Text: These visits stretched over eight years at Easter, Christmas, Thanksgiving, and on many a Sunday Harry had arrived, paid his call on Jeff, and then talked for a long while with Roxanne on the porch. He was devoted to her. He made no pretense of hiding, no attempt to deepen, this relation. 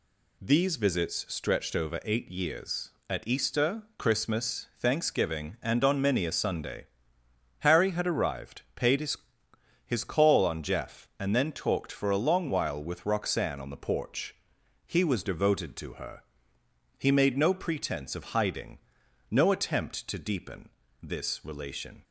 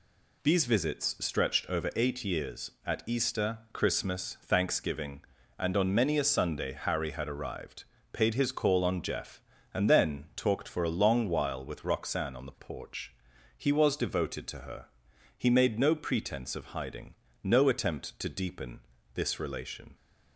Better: second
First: pauses between "Sunday" and "Harry"; noticeable; at 6.8 s; 0.76 s long // says "his" twice; at 9.8 s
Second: none

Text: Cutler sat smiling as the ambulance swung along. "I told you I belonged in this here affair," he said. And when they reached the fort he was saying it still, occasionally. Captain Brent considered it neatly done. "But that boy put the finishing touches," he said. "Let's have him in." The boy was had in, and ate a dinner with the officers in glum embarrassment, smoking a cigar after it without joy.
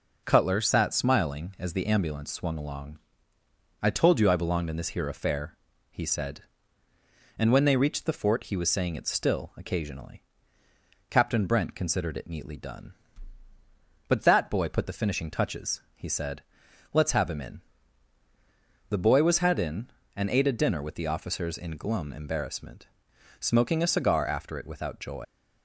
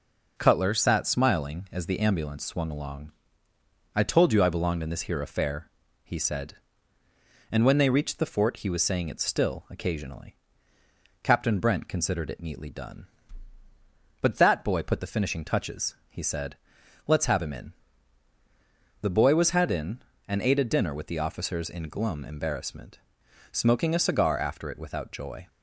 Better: second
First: leaves "joy" unfinished; at 25.2 s; 110 ms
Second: none

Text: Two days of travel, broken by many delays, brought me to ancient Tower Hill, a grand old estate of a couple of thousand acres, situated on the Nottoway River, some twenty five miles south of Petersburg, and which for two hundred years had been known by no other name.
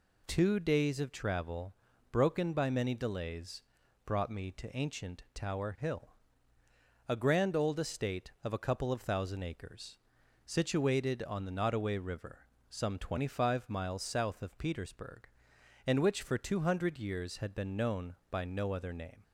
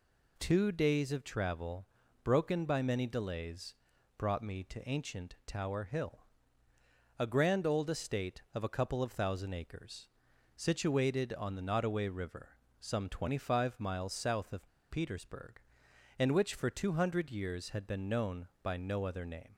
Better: first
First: none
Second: pauses between "of" and "Petersburg"; slight; at 14.6 s; 0.22 s long

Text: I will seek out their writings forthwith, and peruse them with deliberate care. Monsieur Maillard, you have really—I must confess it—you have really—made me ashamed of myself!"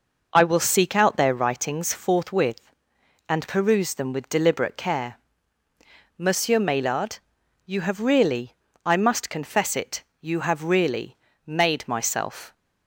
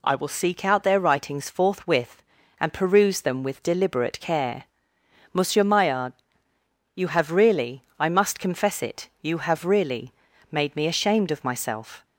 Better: second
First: skips "me ashamed of"; at 11.8 s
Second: none

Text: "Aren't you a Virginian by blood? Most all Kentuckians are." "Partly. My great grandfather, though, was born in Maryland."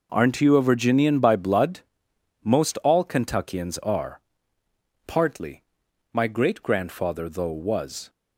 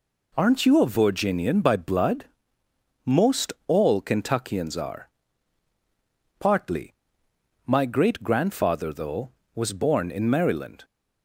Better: second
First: stops before "born in Maryland"; at 8.0 s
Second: none

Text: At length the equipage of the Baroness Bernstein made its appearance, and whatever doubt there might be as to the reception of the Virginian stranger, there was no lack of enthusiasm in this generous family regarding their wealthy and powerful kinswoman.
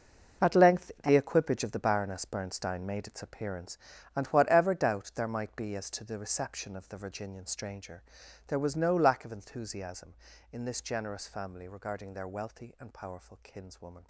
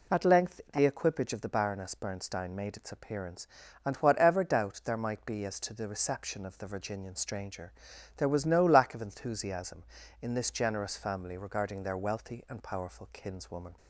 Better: second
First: gets quieter; strong; throughout; 12.5 dB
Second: none

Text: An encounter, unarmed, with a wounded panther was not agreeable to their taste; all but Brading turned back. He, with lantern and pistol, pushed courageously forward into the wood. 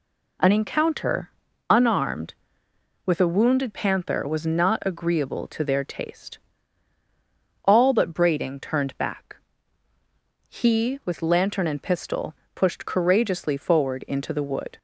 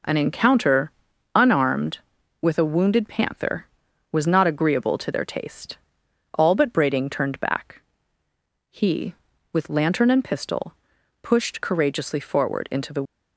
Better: first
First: none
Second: stops before "wood"; at 13.0 s

